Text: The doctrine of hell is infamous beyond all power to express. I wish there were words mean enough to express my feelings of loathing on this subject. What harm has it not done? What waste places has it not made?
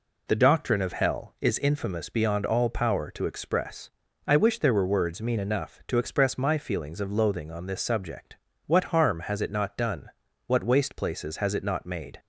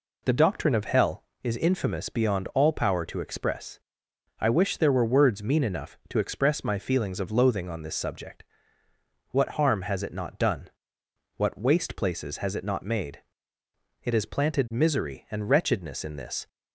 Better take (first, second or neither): first